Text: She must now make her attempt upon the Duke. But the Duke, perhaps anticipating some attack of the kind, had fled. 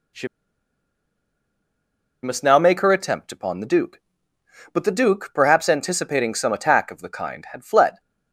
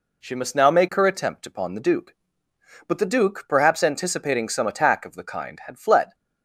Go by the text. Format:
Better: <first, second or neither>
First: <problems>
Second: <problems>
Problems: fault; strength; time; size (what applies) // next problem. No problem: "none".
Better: second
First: pauses between "She" and "must"; strong; at 0.2 s; 1.9 s long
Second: none